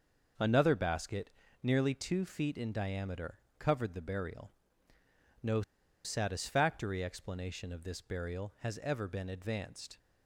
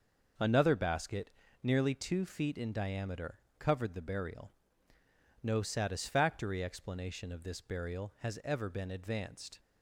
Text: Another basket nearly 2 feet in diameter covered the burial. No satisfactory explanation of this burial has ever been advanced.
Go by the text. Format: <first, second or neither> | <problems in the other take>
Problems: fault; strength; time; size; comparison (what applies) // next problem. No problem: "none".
second | starts louder than the rest; noticeable; until 1.7 s; 6 dB; noticeable in the second // pauses between "basket" and "nearly"; slight; at 1.2 s; 0.34 s long; slight in the second // pauses between "diameter" and "covered"; slight; at 3.3 s; 0.18 s long; slight in the second // pauses between "No" and "satisfactory"; at 5.6 s; 0.43 s long